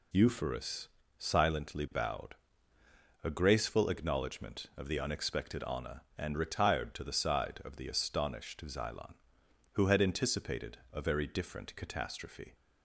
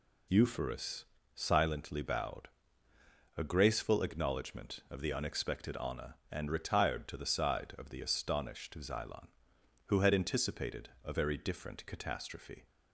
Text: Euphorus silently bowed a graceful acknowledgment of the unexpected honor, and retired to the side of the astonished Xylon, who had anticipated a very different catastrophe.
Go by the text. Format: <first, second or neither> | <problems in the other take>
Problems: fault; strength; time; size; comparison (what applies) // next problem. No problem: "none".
neither | pauses between "Euphorus" and "silently"; slight; the same in both // pauses between "bowed" and "a"; noticeable; the same in both // pauses between "anticipated" and "a"; slight; the same in both